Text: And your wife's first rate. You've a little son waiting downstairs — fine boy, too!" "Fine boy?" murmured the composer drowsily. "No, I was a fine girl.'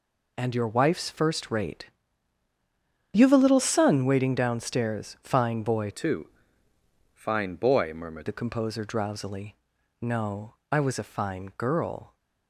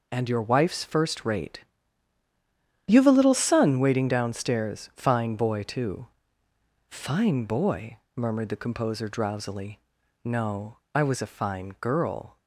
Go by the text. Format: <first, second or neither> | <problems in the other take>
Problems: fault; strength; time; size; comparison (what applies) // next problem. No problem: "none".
second | changes voice from "too" to "murmured"; from 5.9 to 8.2 s; 2.3 s long